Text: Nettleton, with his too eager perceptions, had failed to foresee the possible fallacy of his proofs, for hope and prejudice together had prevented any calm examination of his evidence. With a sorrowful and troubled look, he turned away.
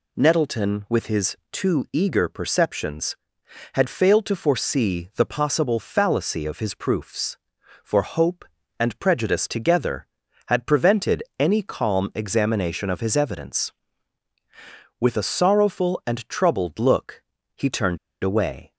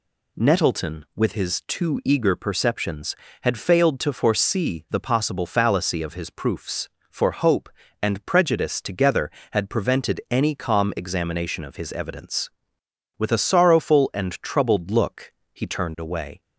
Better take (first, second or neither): second